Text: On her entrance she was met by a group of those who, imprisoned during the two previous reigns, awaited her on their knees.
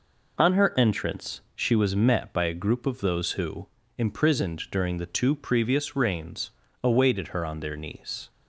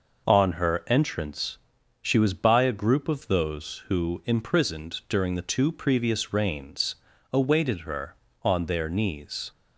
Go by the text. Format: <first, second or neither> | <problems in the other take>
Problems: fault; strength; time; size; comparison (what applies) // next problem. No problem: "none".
first | pauses between "entrance" and "she"; at 1.5 s; 0.42 s long // skips "met"; at 2.3 s